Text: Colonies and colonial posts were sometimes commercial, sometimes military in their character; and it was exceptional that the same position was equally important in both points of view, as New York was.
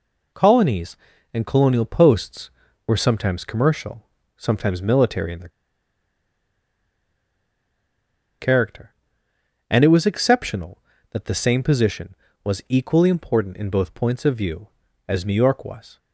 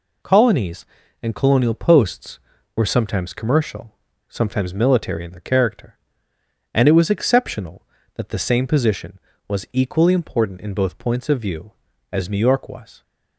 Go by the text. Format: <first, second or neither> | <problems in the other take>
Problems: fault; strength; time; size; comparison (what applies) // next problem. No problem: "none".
second | pauses between "their" and "character"; strong; at 5.4 s; 2.9 s long